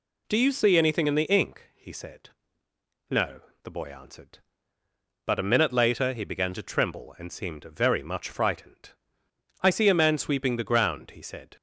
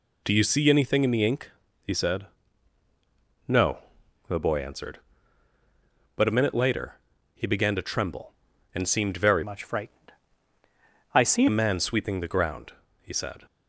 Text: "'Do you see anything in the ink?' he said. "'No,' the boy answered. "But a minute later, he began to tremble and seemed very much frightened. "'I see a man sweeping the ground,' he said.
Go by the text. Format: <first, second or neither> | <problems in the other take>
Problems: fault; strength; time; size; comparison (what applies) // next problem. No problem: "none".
first | changes voice from "much" to "see"; from 9.4 to 11.4 s; 2.0 s long